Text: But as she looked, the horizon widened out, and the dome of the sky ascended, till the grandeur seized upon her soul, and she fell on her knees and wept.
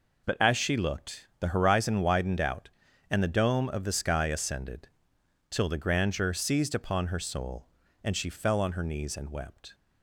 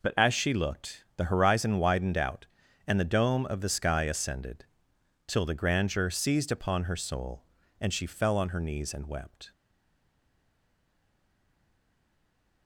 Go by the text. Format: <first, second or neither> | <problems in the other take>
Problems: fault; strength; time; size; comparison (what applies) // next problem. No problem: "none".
first | stays silent after the last word; strong; from 9.5 s on; 3.1 s long